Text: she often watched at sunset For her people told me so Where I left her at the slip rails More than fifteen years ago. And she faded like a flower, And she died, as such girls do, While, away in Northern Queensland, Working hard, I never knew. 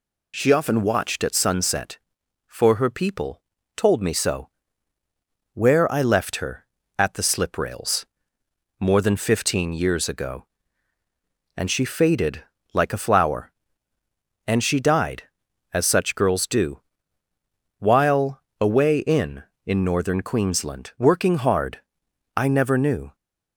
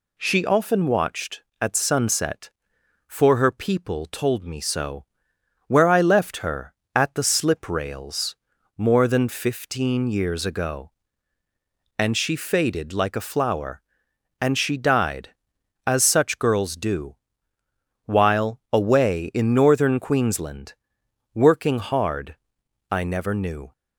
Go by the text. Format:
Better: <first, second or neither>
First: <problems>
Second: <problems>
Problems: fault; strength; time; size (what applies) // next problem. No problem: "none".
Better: second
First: pauses between "people" and "told"; slight; at 3.4 s; 0.36 s long // pauses between "so" and "Where"; at 4.4 s; 1.0 s long // pauses between "rails" and "More"; noticeable; at 8.0 s; 0.76 s long // pauses between "faded" and "like"; slight; at 12.4 s; 0.30 s long // says "in" twice; at 19.6 s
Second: pauses between "so" and "Where"; noticeable; at 5.0 s; 0.62 s long // pauses between "rails" and "More"; at 8.3 s; 0.42 s long